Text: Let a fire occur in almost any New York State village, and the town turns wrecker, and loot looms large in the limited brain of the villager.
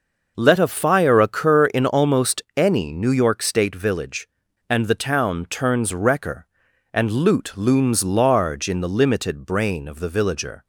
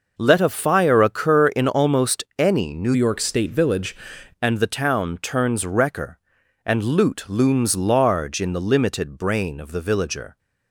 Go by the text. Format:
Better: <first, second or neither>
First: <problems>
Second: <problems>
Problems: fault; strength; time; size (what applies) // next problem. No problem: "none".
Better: first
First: pauses between "almost" and "any"; slight; at 2.4 s; 0.16 s long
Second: pauses between "almost" and "any"; slight; at 2.2 s; 0.16 s long // changes voice from "York" to "village"; from 2.9 to 3.9 s; 1.0 s long